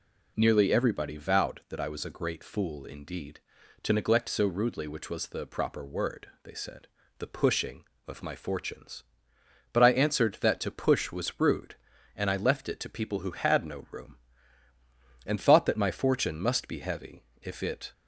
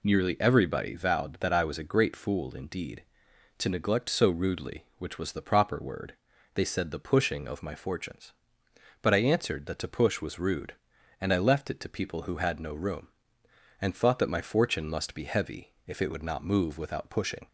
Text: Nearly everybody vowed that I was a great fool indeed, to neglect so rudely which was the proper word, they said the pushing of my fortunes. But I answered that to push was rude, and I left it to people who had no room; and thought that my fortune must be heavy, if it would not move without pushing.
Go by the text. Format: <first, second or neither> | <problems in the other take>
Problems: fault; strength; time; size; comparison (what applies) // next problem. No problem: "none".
second | pauses between "said" and "the"; slight; at 6.8 s; 0.32 s long // stops before "would not move without pushing"; at 17.9 s